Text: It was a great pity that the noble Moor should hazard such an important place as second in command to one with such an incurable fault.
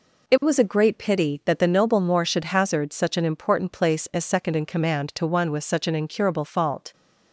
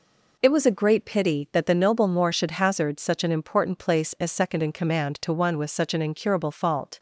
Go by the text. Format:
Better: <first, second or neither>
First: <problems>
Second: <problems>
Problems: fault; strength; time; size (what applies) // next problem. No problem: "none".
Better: neither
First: none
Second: none